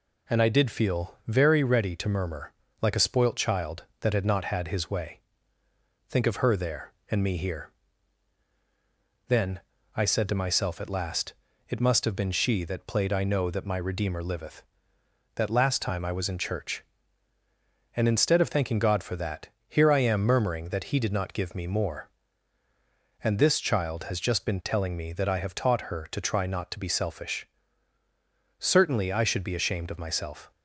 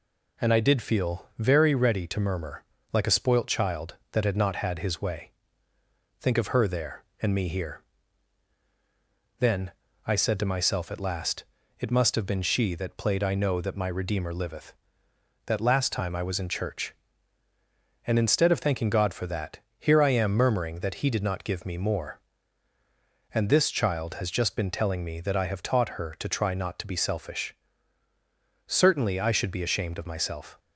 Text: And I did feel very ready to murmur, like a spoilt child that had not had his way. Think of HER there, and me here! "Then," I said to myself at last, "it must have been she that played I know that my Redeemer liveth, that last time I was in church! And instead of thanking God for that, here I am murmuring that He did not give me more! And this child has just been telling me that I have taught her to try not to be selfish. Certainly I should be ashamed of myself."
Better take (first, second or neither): neither